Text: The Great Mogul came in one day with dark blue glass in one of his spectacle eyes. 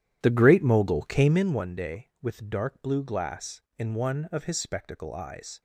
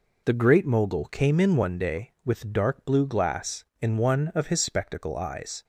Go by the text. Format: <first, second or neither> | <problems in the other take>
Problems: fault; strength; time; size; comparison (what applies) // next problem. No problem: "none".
second | starts louder than the rest; strong; until 1.4 s; 11 dB